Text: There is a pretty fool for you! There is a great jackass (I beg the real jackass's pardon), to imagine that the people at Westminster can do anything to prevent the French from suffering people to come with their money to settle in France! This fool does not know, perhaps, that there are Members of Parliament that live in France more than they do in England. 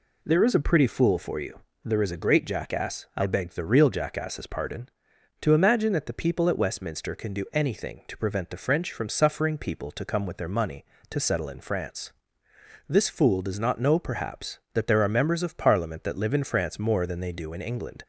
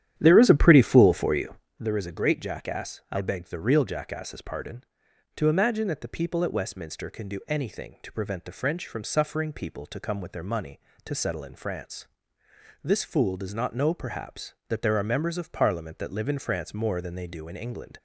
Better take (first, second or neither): first